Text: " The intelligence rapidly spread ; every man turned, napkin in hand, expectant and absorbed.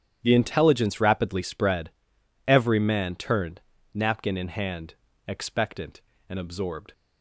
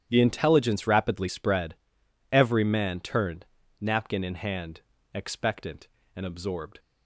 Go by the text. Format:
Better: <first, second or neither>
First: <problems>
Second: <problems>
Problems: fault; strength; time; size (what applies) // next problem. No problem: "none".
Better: neither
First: starts louder than the rest; strong; until 1.2 s; 10 dB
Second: starts louder than the rest; strong; until 1.0 s; 10 dB